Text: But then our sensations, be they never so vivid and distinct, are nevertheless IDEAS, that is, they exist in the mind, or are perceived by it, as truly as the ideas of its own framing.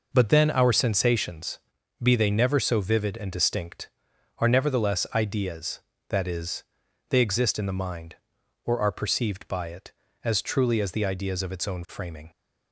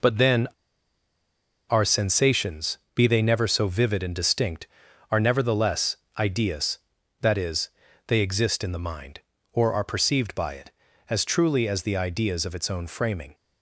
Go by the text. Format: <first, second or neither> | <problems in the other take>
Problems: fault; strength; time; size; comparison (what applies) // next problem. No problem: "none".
first | pauses between "then" and "our"; at 0.4 s; 1.2 s long // pauses between "nevertheless" and "IDEAS"; slight; at 5.9 s; 0.22 s long